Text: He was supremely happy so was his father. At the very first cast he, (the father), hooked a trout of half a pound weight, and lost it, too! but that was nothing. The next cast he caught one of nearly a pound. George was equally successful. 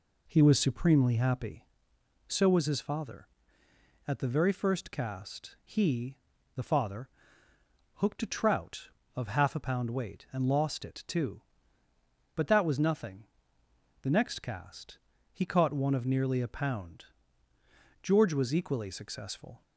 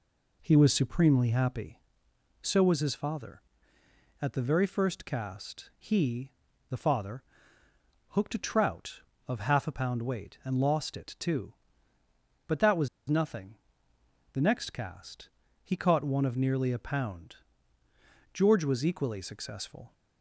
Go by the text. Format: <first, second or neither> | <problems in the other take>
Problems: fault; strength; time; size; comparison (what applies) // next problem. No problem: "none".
first | pauses between "was" and "nothing"; slight; at 12.8 s; 0.21 s long // pauses between "cast" and "he"; slight; at 15.2 s; 0.34 s long; slight in the first